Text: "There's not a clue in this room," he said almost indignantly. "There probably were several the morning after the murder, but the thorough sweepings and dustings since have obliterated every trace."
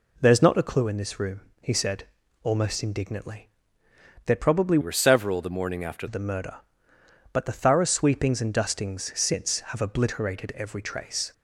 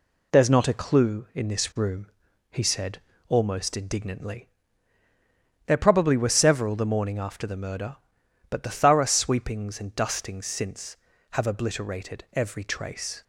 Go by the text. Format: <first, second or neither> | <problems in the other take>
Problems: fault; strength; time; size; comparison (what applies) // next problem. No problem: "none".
second | pauses between "said" and "almost"; slight; at 2.0 s; 0.36 s long; slight in the second // changes voice from "were" to "after"; from 4.8 to 6.0 s; 1.2 s long